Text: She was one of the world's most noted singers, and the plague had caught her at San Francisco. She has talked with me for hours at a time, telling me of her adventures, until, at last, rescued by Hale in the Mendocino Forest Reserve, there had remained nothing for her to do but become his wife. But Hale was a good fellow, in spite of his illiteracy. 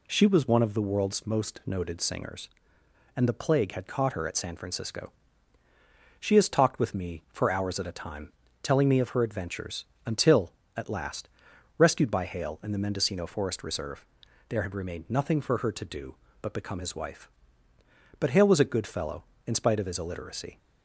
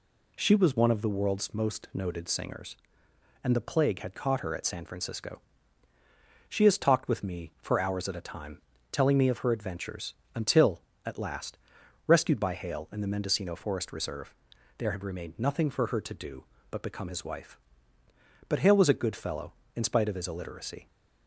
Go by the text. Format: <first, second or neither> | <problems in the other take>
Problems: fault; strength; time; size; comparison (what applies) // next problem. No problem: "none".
neither | none